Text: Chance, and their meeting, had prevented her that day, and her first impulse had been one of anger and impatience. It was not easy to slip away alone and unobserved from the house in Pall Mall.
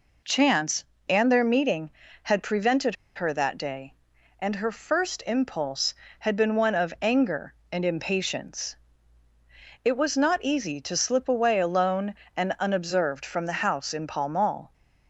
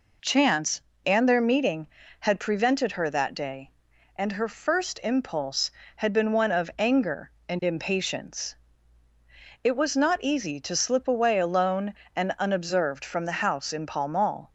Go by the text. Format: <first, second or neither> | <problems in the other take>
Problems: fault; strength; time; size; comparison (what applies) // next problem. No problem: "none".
second | pauses between "prevented" and "her"; slight; at 2.9 s; 0.21 s long